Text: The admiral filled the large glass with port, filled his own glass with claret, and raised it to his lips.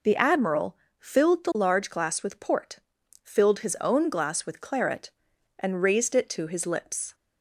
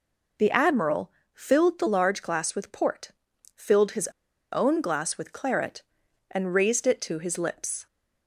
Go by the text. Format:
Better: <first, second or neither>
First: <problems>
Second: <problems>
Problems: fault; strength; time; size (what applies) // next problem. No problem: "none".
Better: first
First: pauses between "admiral" and "filled"; slight; at 0.7 s; 0.24 s long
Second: pauses between "admiral" and "filled"; slight; at 1.1 s; 0.24 s long // pauses between "his" and "own"; at 4.0 s; 0.43 s long